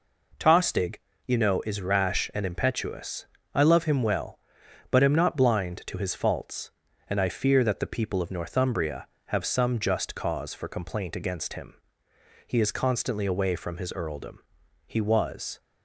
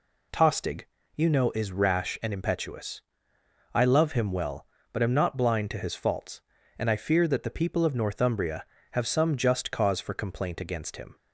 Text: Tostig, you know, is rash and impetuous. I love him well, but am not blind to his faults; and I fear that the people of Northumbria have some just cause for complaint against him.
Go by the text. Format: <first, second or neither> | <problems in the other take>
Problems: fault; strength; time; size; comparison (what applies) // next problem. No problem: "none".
second | goes on to say "He is constantly away from his earldom He was"; strong; from 12.4 s on; 3.1 s long